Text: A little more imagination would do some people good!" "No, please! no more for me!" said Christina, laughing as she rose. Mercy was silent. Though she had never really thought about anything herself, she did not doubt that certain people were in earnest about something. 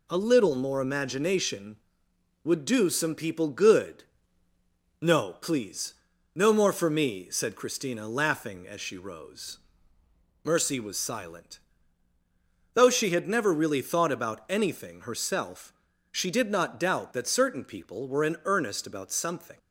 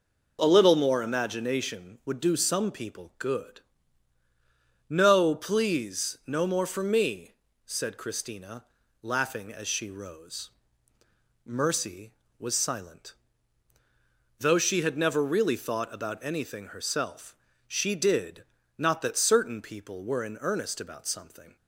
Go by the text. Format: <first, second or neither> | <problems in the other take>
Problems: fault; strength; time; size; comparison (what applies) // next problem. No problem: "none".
first | pauses between "did" and "not"; slight; at 18.4 s; 0.34 s long // skips "doubt"; at 19.0 s